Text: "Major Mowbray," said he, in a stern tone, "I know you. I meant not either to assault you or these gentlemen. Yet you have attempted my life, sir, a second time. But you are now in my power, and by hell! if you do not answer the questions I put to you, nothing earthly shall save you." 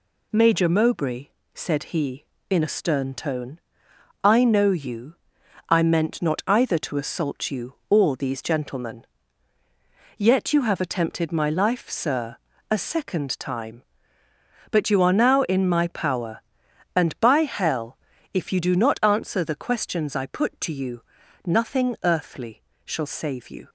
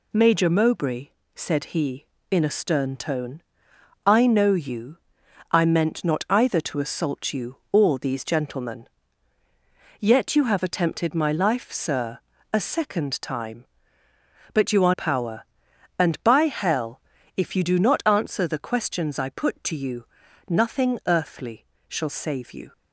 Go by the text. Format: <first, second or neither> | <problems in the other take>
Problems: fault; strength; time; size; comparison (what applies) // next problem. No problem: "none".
first | skips "now in my"; at 14.9 s // pauses between "earthly" and "shall"; slight; at 21.6 s; 0.24 s long; slight in the first